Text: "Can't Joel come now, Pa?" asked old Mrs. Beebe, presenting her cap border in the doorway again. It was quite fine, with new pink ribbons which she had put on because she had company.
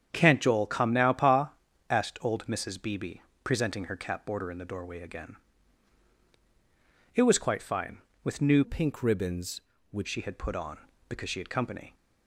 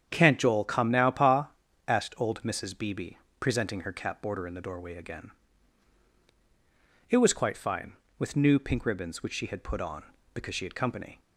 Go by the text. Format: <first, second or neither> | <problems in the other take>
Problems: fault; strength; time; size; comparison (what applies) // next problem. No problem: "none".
second | starts louder than the rest; strong; until 1.1 s; 8.5 dB; strong in the second // changes voice from "pink" to "which"; from 8.6 to 10.0 s; 1.4 s long